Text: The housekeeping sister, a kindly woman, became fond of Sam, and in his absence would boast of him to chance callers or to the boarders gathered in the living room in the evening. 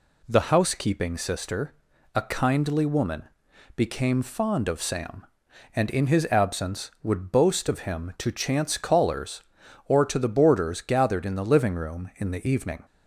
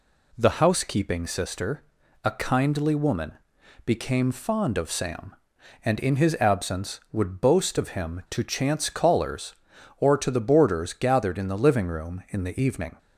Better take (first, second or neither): neither